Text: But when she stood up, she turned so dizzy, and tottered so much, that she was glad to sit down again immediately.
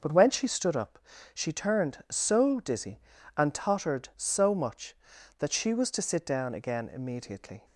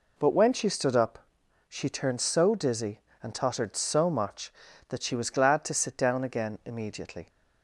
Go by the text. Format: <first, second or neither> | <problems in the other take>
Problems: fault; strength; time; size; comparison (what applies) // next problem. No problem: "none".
second | starts louder than the rest; noticeable; until 1.3 s; 6 dB // skips "glad"; at 5.9 s